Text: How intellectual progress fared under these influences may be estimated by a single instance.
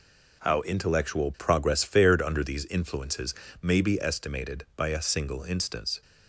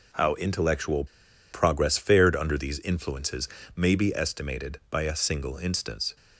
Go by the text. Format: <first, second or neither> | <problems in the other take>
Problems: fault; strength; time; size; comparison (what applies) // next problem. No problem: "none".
first | pauses between "intellectual" and "progress"; noticeable; at 1.0 s; 0.47 s long // pauses between "influences" and "may"; slight; at 3.4 s; 0.28 s long; slight in the first